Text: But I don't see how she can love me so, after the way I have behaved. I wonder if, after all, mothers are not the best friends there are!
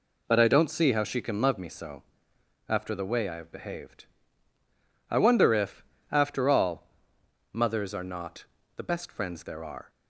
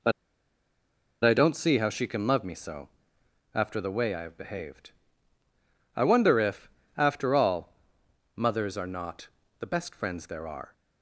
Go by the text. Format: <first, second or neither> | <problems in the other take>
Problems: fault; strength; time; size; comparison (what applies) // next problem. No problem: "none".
first | pauses between "But" and "I"; at 0.1 s; 1.1 s long // pauses between "not" and "the"; slight; at 9.2 s; 0.32 s long; slight in the first